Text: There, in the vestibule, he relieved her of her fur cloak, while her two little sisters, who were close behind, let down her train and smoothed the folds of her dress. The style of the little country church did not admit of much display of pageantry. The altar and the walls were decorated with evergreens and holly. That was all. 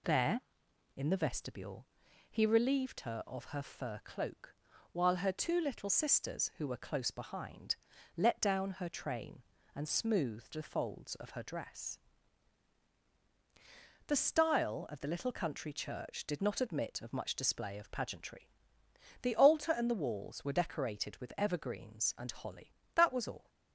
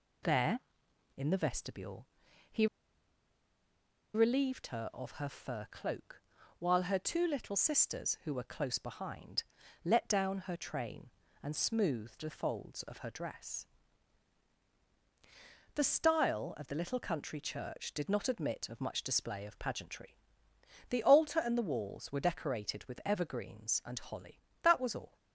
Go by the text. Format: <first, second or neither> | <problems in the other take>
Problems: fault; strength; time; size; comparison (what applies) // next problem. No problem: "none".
first | pauses between "he" and "relieved"; strong; at 2.6 s; 1.4 s long